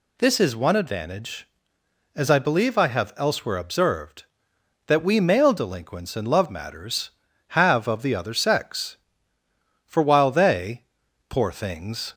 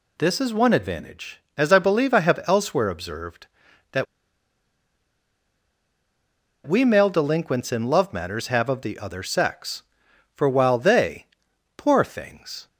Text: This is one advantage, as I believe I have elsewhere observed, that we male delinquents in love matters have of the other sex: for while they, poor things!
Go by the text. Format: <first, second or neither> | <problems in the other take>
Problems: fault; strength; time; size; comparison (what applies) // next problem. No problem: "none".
first | pauses between "that" and "we"; strong; at 4.0 s; 2.6 s long